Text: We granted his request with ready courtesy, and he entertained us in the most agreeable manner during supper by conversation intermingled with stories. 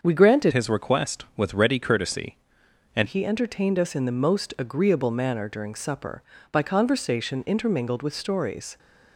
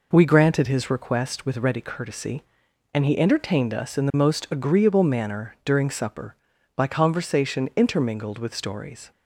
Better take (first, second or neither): second